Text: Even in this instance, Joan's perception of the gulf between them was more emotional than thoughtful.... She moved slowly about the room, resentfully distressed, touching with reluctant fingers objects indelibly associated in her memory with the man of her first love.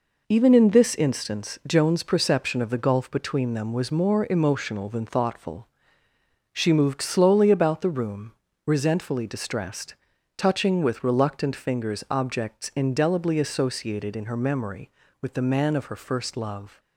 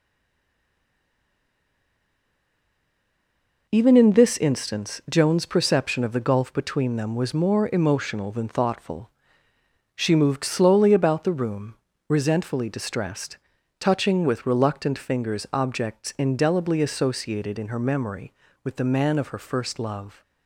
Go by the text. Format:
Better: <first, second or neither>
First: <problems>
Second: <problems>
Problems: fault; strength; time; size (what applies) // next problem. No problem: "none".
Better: first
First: none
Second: stays silent before the first word; strong; until 3.6 s; 3.6 s long